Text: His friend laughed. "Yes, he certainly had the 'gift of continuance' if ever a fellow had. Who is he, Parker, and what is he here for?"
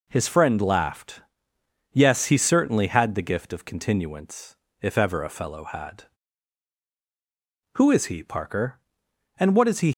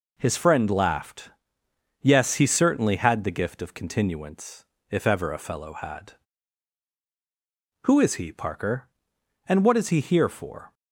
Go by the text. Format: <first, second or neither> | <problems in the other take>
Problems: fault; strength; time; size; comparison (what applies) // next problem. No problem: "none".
second | pauses between "continuance" and "if"; slight; at 4.5 s; 0.24 s long; slight in the second // stops before "here for"; at 9.9 s